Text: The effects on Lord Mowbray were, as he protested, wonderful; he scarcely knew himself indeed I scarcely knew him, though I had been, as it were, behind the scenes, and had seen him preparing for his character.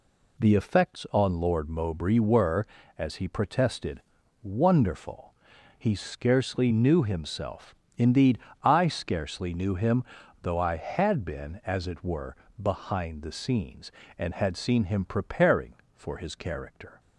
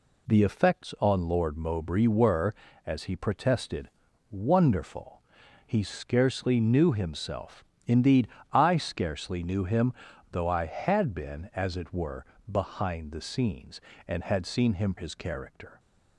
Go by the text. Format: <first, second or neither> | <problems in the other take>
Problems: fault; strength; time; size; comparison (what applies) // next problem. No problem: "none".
first | pauses between "himself" and "indeed"; slight; at 7.6 s; 0.22 s long; slight in the first // pauses between "indeed" and "I"; slight; at 8.2 s; 0.24 s long; slight in the first // skips "preparing for"; at 14.9 s